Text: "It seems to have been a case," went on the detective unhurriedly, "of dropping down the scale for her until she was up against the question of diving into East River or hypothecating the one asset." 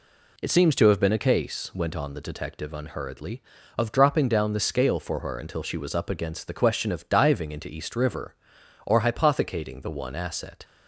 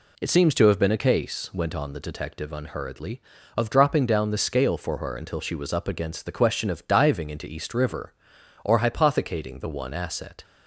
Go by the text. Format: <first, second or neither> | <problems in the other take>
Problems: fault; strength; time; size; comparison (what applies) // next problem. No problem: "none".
neither | none